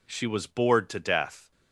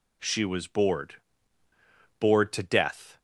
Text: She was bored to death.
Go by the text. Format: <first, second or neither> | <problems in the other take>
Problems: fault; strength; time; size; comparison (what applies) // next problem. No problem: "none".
first | says "bored" twice; at 2.1 s